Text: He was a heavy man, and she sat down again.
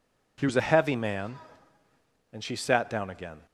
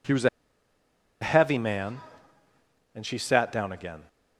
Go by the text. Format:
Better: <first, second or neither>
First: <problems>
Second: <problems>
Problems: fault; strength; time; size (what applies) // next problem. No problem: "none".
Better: first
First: none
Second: pauses between "a" and "heavy"; noticeable; at 0.2 s; 0.92 s long